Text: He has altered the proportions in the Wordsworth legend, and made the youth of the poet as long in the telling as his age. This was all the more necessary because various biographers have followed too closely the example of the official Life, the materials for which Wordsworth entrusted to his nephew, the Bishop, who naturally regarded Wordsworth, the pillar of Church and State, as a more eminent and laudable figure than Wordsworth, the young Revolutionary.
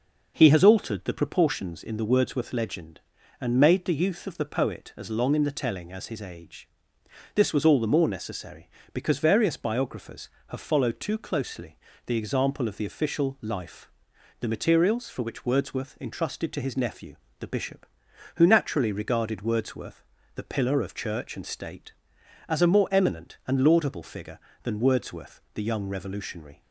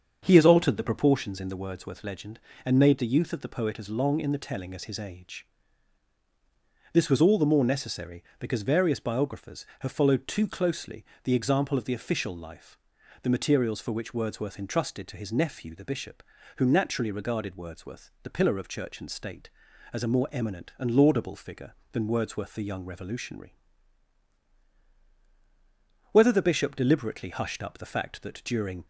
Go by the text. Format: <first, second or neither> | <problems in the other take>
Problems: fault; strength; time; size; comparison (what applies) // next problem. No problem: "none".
first | starts louder than the rest; until 1.2 s; 7 dB // pauses between "closely" and "the"; slight; at 11.0 s; 0.20 s long; slight in the first // goes on to say "Whether the Bishop deliberately hushed up the fact that during"; strong; from 26.1 s on; 2.7 s long